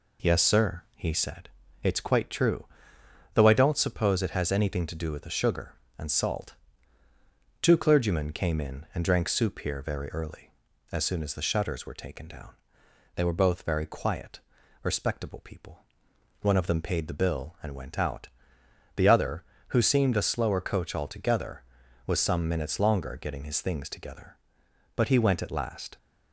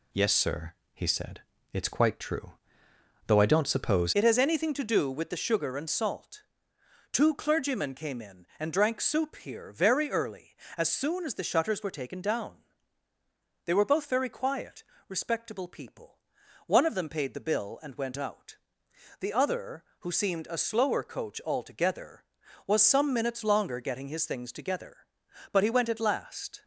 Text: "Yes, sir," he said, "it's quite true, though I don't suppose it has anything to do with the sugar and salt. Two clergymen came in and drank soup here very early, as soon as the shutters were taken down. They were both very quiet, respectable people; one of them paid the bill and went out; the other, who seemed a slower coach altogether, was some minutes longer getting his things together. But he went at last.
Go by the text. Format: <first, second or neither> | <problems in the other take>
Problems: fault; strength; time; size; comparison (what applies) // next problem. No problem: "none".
first | changes voice at "it"; from 4.1 s on; 22.5 s long